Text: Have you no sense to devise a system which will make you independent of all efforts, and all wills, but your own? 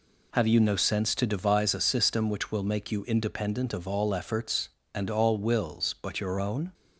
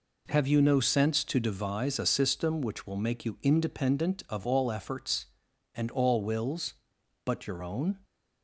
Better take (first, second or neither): neither